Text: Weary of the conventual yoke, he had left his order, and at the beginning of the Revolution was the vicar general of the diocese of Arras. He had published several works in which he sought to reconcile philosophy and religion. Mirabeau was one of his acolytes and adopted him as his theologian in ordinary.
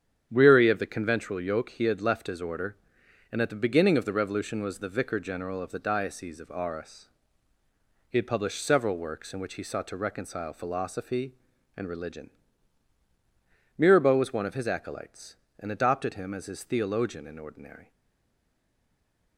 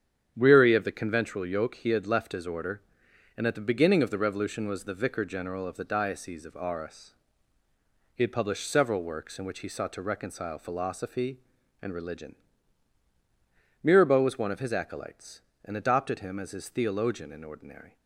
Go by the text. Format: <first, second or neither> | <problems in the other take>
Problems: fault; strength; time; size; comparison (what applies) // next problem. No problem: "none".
second | starts louder than the rest; strong; until 1.3 s; 8.5 dB; strong in the second // stays silent after the last word; noticeable; from 17.9 s on; 1.4 s long